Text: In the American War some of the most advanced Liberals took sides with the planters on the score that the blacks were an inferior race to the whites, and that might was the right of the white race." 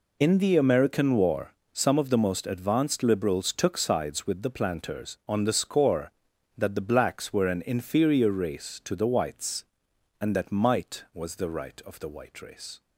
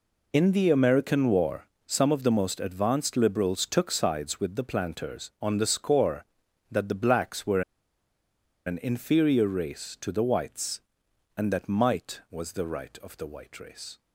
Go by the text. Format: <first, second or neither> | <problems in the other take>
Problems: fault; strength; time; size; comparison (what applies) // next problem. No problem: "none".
first | pauses between "War" and "some"; slight; at 1.6 s; 0.18 s long; slight in the first // pauses between "were" and "an"; at 7.6 s; 1.0 s long